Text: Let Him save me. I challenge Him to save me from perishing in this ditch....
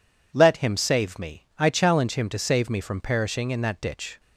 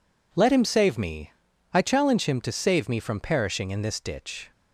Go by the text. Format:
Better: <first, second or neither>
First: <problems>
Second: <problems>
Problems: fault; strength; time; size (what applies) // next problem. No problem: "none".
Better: second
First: says "that" for "this"; at 3.6 s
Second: none